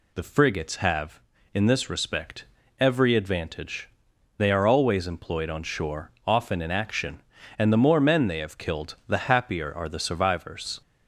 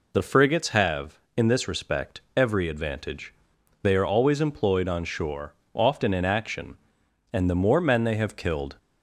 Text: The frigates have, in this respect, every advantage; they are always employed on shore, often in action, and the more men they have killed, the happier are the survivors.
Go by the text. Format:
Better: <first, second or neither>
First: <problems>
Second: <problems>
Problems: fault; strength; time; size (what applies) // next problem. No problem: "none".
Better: first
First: none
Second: stops before "the happier are the survivors"; at 8.7 s